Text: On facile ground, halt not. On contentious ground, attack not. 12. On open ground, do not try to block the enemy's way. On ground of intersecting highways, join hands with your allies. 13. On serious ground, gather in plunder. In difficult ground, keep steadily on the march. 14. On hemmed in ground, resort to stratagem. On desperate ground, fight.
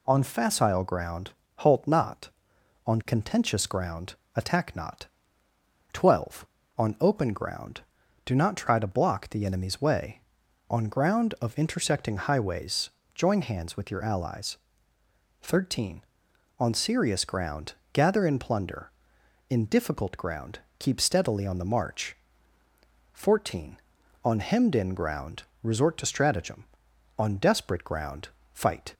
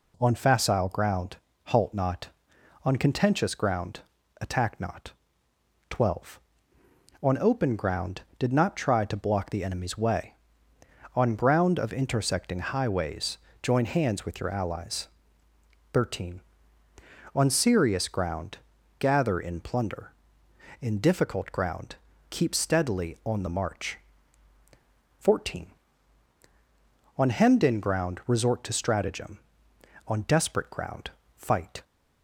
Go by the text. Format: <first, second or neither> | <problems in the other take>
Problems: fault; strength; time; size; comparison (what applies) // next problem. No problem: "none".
first | says "did" for "do"; at 8.3 s